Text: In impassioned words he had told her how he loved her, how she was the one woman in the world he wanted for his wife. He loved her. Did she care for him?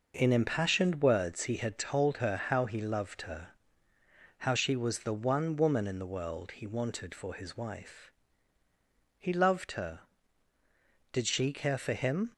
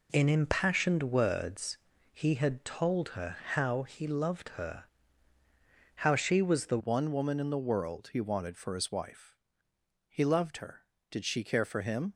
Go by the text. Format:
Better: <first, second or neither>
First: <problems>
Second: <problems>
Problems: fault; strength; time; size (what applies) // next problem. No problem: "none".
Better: first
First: none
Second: pauses between "words" and "he"; slight; at 1.7 s; 0.36 s long // pauses between "her" and "how"; slight; at 3.3 s; 0.16 s long // changes voice at "one"; from 6.7 s on; 5.4 s long